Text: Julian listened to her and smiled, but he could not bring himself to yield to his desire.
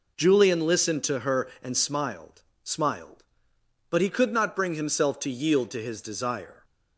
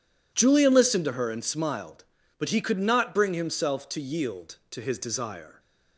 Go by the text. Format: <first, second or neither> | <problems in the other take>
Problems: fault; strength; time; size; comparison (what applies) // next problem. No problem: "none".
second | says "smiled" twice; at 2.6 s